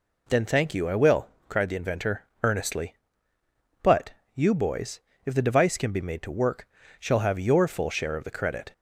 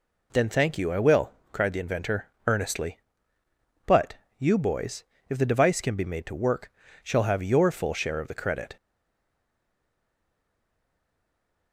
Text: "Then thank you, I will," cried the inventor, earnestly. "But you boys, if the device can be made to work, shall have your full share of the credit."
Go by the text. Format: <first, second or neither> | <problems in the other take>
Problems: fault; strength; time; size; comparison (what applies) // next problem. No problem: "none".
first | pauses between "But" and "you"; slight; at 4.1 s; 0.24 s long; slight in the first // stays silent after the last word; strong; from 8.7 s on; 3.0 s long